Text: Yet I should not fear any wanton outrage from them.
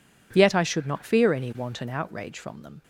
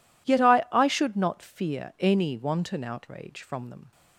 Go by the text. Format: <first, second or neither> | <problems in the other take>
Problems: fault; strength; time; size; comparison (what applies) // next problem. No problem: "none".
first | says "I" twice; at 0.7 s